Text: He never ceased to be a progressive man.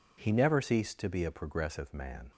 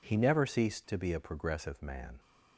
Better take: neither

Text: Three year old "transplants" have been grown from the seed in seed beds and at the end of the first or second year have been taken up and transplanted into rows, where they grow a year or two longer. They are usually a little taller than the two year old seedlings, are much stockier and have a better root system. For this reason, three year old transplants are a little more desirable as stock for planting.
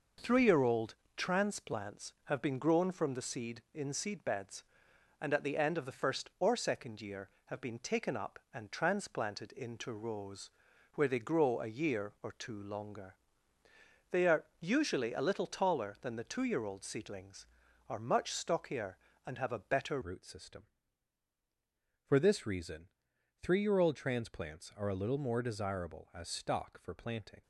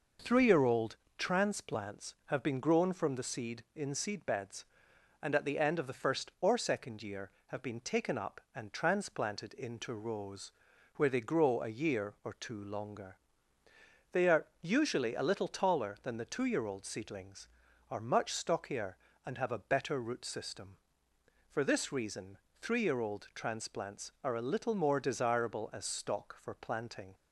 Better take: second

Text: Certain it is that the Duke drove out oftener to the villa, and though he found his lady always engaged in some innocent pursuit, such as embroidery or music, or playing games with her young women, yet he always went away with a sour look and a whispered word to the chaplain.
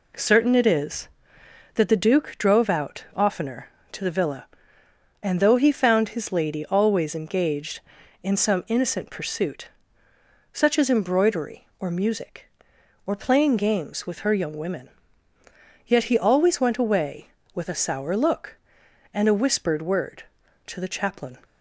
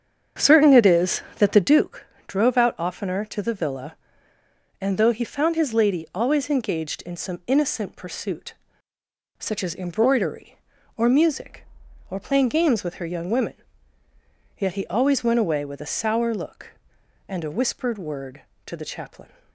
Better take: first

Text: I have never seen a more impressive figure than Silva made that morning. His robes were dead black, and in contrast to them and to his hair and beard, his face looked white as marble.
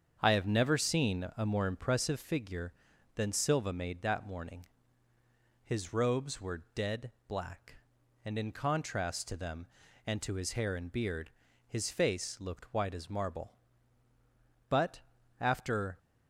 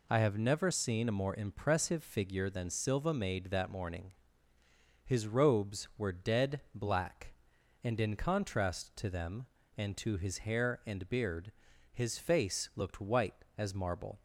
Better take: second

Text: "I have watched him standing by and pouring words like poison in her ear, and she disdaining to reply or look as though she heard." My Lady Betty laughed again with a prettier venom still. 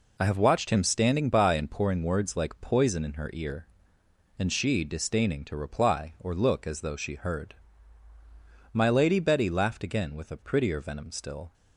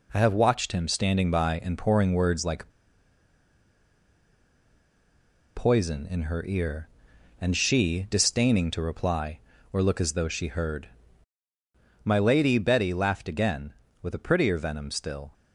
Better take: first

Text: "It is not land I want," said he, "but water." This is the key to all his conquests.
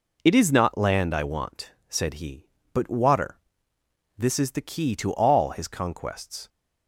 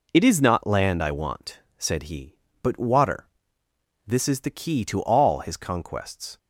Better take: neither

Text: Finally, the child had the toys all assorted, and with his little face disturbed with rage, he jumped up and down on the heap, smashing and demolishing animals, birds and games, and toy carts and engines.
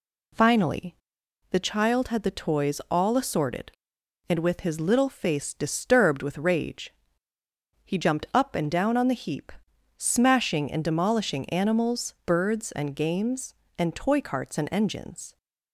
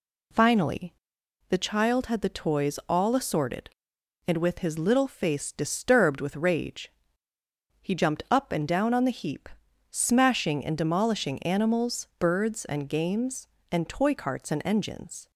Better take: neither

